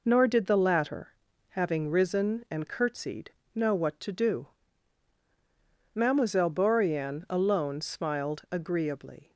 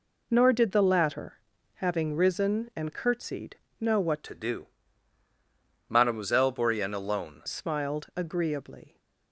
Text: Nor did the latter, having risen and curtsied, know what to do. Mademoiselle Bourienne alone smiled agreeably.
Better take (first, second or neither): first